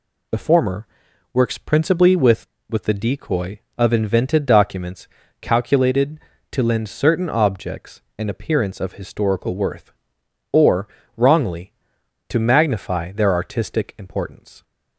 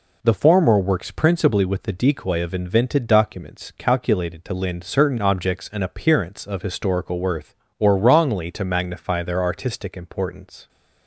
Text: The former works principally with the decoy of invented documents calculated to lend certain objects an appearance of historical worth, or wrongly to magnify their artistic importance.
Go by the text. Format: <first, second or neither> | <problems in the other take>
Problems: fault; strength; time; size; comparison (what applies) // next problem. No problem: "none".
second | pauses between "former" and "works"; noticeable; at 0.8 s; 0.46 s long // says "with" twice; at 2.6 s // pauses between "documents" and "calculated"; slight; at 5.0 s; 0.32 s long // pauses between "objects" and "an"; slight; at 8.0 s; 0.18 s long // pauses between "or" and "wrongly"; slight; at 10.8 s; 0.26 s long